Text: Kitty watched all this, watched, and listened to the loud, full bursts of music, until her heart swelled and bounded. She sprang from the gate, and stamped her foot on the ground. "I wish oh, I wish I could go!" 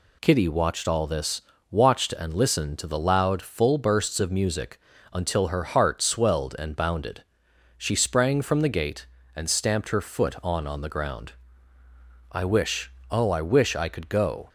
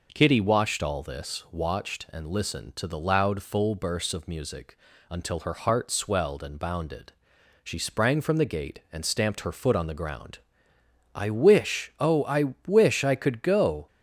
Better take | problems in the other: second | says "on" twice; at 10.6 s // pauses between "wish" and "oh"; slight; at 12.9 s; 0.18 s long

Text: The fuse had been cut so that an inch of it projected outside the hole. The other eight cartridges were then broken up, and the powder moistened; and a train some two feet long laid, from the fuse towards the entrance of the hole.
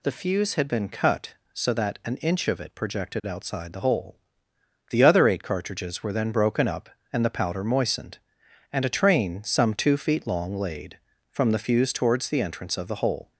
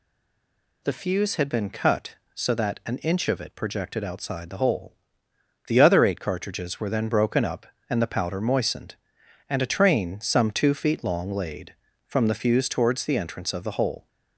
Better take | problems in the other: first | stays silent before the first word; slight; until 0.8 s; 0.8 s long

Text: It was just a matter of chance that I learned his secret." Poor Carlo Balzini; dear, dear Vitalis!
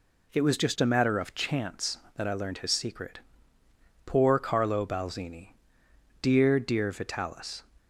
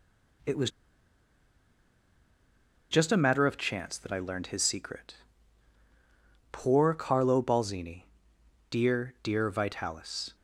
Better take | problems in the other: first | pauses between "was" and "just"; strong; at 0.7 s; 2.2 s long

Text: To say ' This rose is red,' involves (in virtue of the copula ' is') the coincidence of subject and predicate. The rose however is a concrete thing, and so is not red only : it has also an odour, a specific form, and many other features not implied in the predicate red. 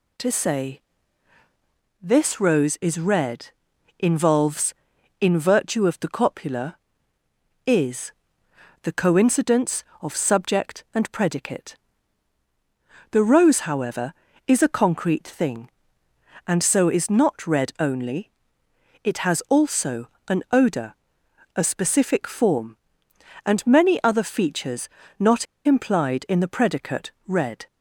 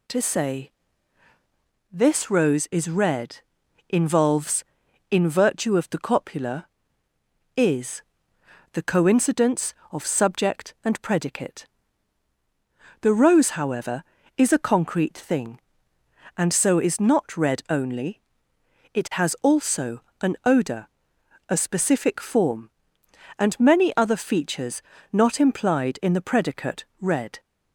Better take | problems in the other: second | pauses between "also" and "an"; slight; at 20.0 s; 0.20 s long; slight in the second // pauses between "features" and "not"; slight; at 24.8 s; 0.30 s long; slight in the second // pauses between "not" and "implied"; slight; at 25.4 s; 0.20 s long

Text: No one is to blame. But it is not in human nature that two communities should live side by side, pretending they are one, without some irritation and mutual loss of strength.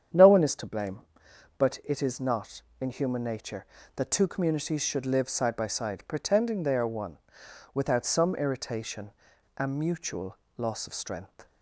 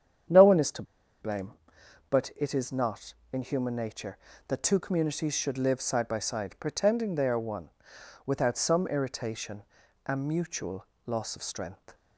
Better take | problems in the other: first | starts louder than the rest; strong; until 2.2 s; 8.5 dB; strong in the first // pauses between "to" and "blame"; at 0.8 s; 0.38 s long // pauses between "mutual" and "loss"; slight; at 10.8 s; 0.22 s long; slight in the first

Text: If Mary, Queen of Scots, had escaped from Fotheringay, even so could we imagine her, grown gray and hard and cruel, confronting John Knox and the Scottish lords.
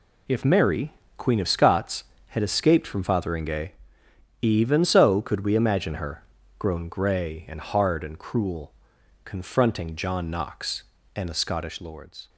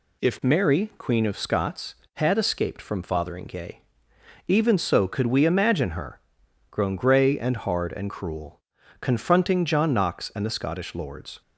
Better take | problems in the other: neither | none

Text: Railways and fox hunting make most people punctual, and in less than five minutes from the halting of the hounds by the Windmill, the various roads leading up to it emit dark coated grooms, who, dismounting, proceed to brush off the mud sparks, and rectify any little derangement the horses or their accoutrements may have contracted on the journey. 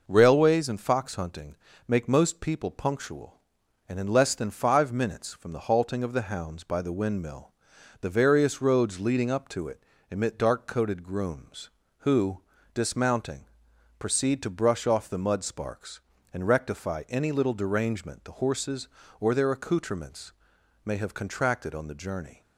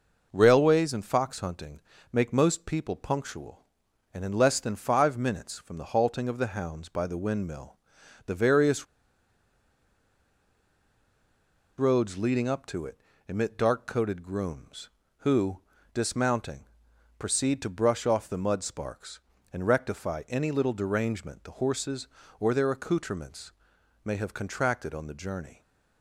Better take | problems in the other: first | pauses between "hunting" and "make"; slight; at 1.8 s; 0.32 s long; slight in the first // pauses between "various" and "roads"; strong; at 8.8 s; 2.9 s long // pauses between "it" and "emit"; slight; at 12.9 s; 0.30 s long; slight in the first // pauses between "accoutrements" and "may"; noticeable; at 23.5 s; 0.52 s long; noticeable in the first

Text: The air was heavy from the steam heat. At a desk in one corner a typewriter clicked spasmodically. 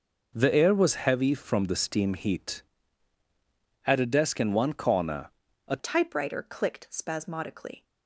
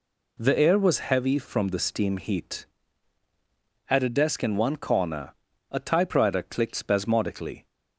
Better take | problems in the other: second | pauses between "corner" and "a"; at 5.2 s; 0.38 s long; also in the second // changes voice at "typewriter"; from 5.7 s on; 2.1 s long

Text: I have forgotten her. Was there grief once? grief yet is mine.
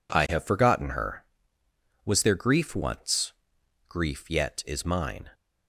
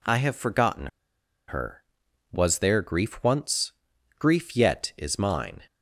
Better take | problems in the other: first | pauses between "forgotten" and "her"; noticeable; at 0.8 s; 0.61 s long

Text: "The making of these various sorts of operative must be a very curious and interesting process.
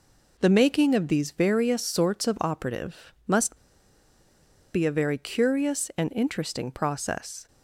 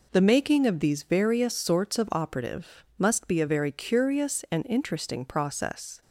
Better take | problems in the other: second | pauses between "must" and "be"; at 3.5 s; 1.1 s long

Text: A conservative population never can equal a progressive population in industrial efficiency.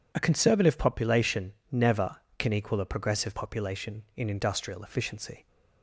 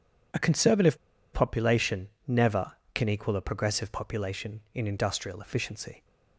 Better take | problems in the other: first | pauses between "conservative" and "population"; at 0.9 s; 0.37 s long // pauses between "population" and "never"; slight; at 2.0 s; 0.18 s long; slight in the first

